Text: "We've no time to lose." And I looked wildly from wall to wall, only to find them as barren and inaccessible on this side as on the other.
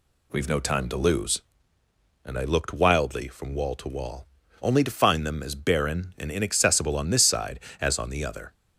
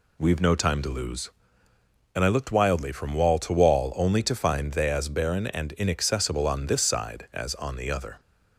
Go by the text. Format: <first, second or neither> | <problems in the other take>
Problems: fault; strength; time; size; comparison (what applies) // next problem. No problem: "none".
first | says "they" for "them"; at 4.7 s